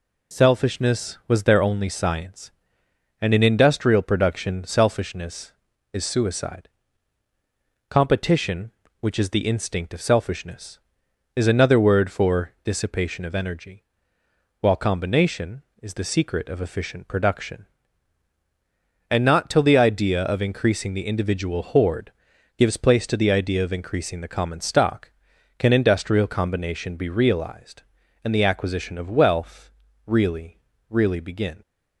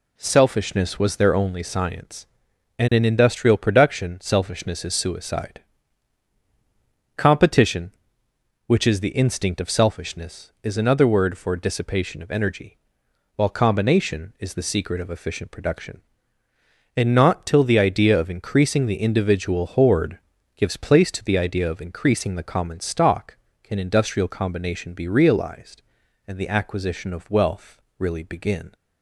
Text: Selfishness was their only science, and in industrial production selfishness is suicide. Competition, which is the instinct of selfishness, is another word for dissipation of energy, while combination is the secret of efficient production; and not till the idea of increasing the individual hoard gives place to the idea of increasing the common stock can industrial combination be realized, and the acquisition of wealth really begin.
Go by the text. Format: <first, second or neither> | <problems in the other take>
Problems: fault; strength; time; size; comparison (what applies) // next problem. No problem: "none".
second | pauses between "hoard" and "gives"; at 22.1 s; 0.44 s long; also in the second // pauses between "wealth" and "really"; slight; at 29.7 s; 0.34 s long; slight in the second // says "really" twice; at 30.8 s